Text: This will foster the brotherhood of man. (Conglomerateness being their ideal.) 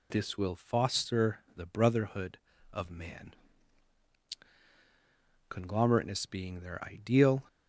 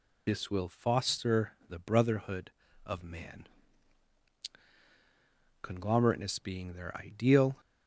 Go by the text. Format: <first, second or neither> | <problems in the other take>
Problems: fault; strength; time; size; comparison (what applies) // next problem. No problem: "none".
first | loses the start of "This"; at 0.2 s; 40 ms // pauses between "foster" and "the"; slight; at 1.5 s; 0.16 s long; slight in the first